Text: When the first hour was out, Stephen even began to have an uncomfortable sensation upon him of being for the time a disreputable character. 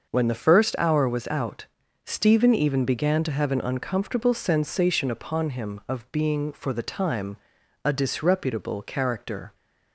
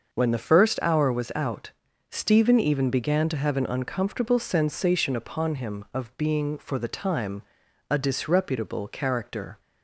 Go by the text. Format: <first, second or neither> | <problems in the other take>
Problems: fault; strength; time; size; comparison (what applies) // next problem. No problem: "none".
neither | starts louder than the rest; the same in both // pauses between "time" and "a"; noticeable; the same in both